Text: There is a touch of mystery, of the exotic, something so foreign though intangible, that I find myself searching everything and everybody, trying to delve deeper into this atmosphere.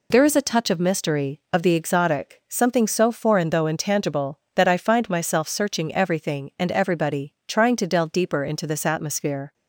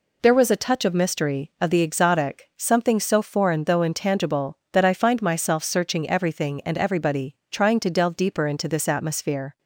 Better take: first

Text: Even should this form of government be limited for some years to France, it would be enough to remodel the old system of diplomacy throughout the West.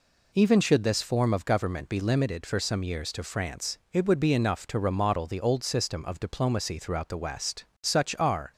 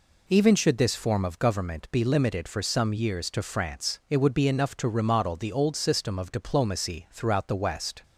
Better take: second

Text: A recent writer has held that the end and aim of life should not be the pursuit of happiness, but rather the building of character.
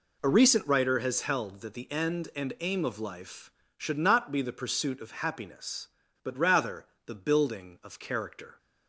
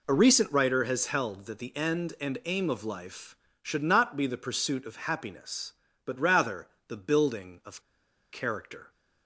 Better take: first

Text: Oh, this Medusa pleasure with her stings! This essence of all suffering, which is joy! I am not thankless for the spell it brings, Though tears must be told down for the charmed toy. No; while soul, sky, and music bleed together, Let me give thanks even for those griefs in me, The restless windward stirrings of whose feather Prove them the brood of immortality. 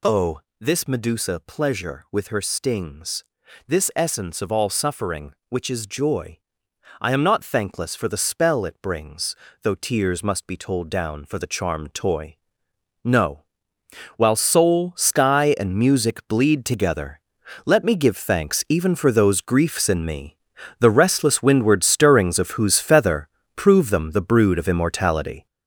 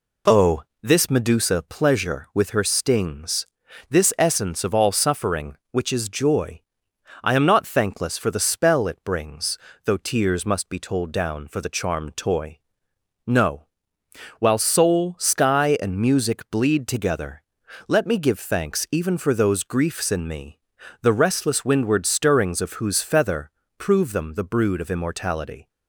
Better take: second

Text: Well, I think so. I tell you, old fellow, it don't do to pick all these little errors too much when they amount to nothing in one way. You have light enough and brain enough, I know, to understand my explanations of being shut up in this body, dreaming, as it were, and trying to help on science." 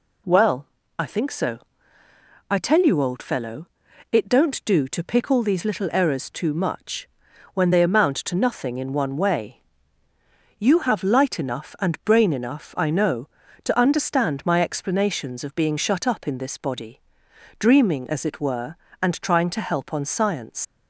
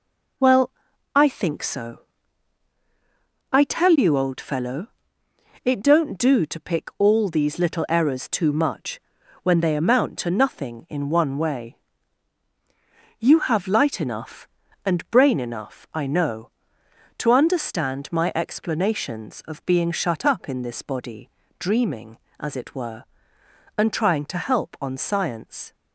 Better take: second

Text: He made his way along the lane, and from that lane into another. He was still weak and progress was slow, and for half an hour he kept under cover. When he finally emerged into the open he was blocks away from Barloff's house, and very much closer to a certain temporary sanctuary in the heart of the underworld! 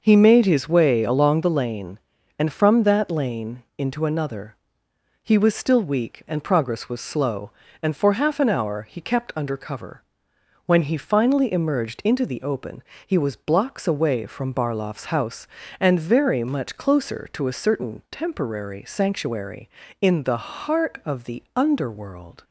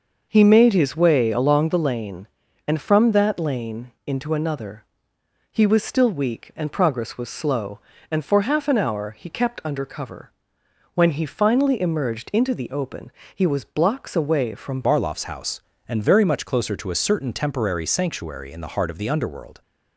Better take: first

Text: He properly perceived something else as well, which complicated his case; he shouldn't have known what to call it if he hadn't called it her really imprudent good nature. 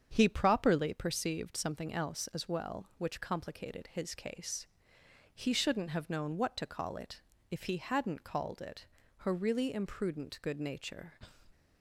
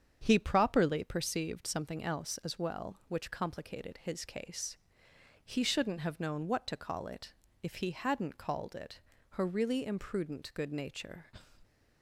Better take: neither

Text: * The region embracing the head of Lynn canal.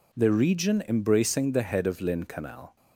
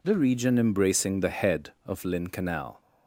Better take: neither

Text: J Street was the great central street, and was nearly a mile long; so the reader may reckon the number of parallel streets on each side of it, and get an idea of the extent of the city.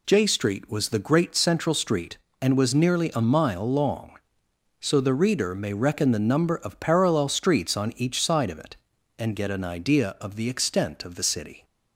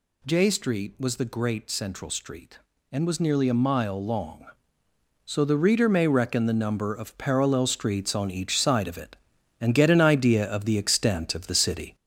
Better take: first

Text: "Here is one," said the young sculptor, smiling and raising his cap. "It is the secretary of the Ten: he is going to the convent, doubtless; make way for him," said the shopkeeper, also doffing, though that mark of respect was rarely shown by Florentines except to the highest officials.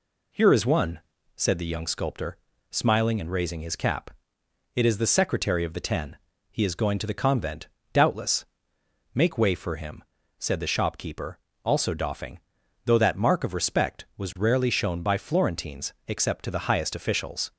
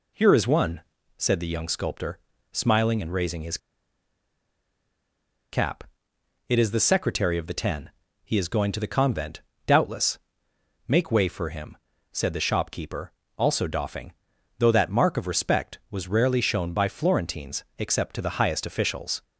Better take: first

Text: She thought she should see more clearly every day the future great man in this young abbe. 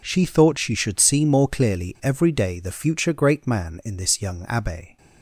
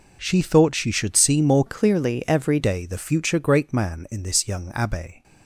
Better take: first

